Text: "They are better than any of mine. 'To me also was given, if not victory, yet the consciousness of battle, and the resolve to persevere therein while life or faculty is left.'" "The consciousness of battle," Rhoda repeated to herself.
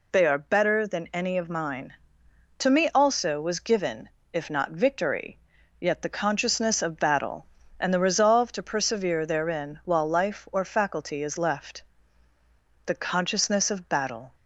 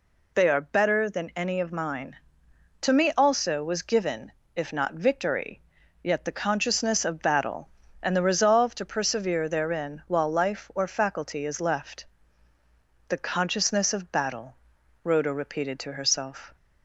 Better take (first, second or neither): second